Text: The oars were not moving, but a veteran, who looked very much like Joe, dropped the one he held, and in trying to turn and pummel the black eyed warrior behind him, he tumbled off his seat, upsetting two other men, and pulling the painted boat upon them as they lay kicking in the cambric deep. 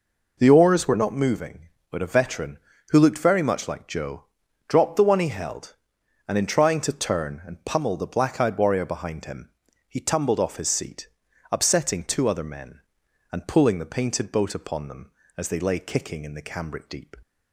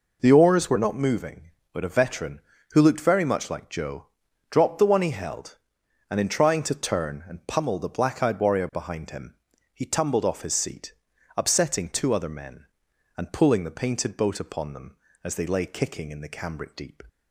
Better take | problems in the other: neither | none

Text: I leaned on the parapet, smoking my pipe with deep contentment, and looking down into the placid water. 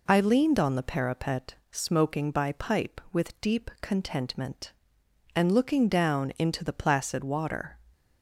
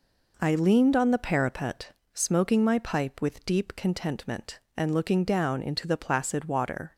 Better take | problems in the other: second | says "by" for "my"; at 2.2 s

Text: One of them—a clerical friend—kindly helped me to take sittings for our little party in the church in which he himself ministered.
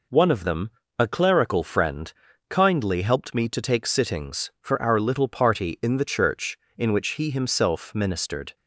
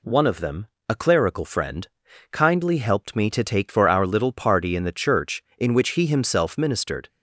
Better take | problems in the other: first | skips "sittings"; at 3.6 s

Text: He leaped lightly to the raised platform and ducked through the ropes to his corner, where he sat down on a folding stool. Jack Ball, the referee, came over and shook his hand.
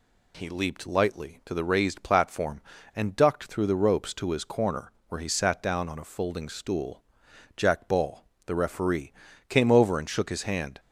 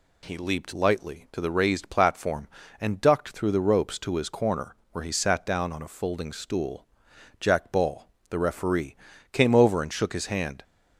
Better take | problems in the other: neither | none

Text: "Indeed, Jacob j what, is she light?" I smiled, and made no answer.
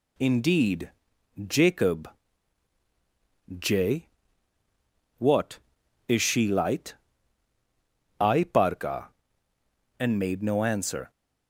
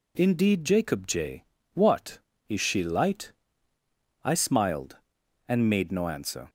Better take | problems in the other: second | pauses between "Jacob" and "j"; strong; at 2.0 s; 1.5 s long // pauses between "j" and "what"; at 4.0 s; 1.1 s long; slight in the second // says "parka" for "smiled"; at 8.4 s

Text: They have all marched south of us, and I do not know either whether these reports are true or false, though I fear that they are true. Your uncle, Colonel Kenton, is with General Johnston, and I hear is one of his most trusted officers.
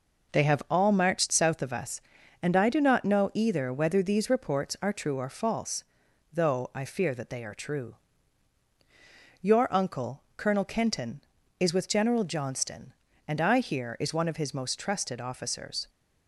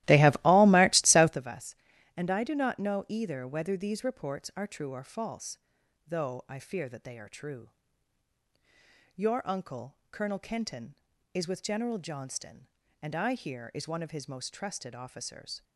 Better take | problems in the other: first | starts louder than the rest; strong; until 1.4 s; 16 dB

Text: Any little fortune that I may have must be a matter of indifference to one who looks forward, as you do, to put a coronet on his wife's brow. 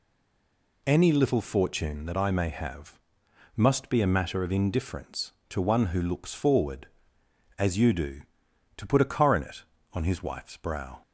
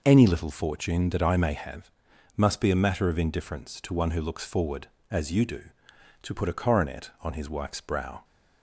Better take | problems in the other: second | stays silent before the first word; slight; until 0.8 s; 0.8 s long // pauses between "have" and "must"; noticeable; at 2.9 s; 0.58 s long; also in the second

